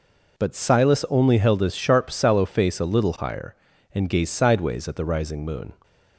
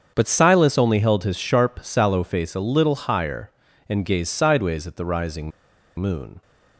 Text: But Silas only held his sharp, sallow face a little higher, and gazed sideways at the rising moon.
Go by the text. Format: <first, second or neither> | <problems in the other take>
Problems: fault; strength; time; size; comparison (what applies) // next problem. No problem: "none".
first | starts louder than the rest; strong; until 1.1 s; 7.5 dB // pauses between "rising" and "moon"; noticeable; at 5.5 s; 0.48 s long